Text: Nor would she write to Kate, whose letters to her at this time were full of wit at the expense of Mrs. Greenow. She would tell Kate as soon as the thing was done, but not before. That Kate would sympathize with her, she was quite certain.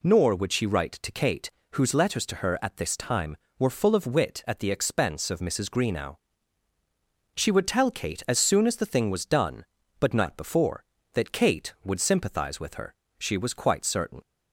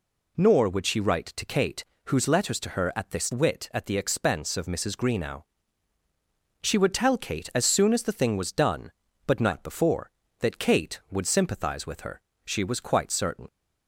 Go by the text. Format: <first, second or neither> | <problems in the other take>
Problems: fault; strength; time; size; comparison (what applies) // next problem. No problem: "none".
first | skips "time were full of"; at 3.3 s